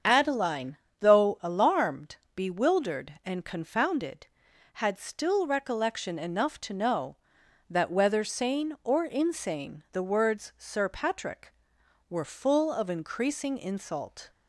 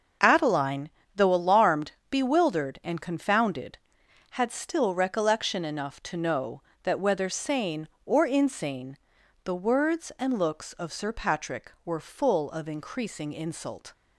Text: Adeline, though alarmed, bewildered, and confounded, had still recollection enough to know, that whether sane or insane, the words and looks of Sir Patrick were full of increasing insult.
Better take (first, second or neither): second